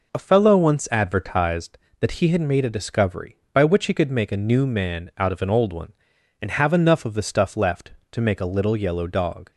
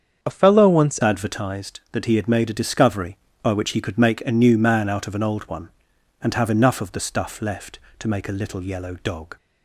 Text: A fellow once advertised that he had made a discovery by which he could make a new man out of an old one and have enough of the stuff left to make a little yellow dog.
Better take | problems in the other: first | starts louder than the rest; strong; until 1.2 s; 7.5 dB // changes voice at "advertised"; from 1.0 s on; 8.3 s long

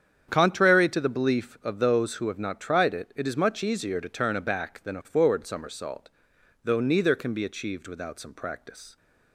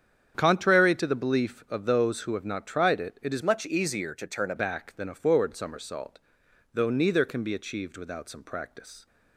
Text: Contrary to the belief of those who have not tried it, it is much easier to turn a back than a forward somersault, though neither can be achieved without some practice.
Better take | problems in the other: first | starts louder than the rest; strong; until 1.3 s; 8 dB; strong in the first // changes voice from "much" to "a"; from 3.4 to 4.5 s; 1.1 s long

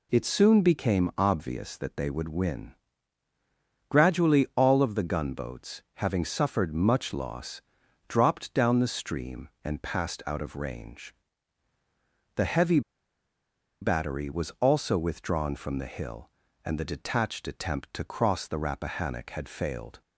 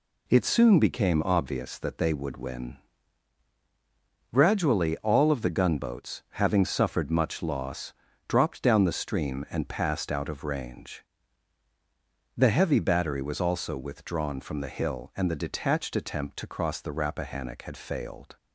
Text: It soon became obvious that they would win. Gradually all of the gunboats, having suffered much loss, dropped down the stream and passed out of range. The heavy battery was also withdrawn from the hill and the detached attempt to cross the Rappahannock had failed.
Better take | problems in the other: second | pauses between "heavy" and "battery"; at 12.8 s; 1.0 s long

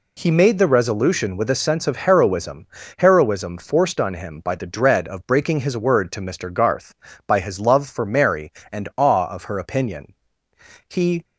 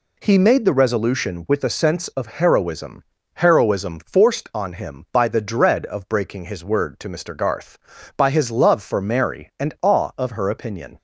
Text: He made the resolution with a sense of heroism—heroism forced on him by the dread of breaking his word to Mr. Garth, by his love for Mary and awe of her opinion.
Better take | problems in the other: second | goes on to say "He"; slight; from 10.8 s on; 0.36 s long

